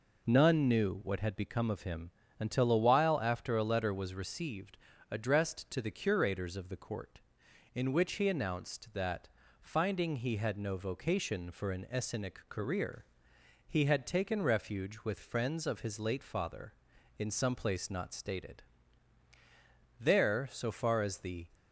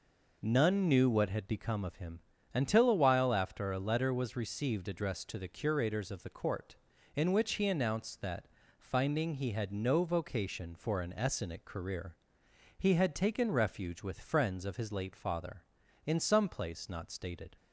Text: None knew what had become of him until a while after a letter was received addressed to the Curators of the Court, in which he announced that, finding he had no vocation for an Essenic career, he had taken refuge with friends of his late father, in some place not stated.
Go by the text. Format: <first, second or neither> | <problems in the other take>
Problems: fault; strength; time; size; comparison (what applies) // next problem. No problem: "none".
second | pauses between "him" and "until"; slight; at 2.1 s; 0.30 s long; slight in the second // pauses between "received" and "addressed"; slight; at 4.7 s; 0.32 s long // goes on to say "There so far as the"; from 19.9 s on; 1.4 s long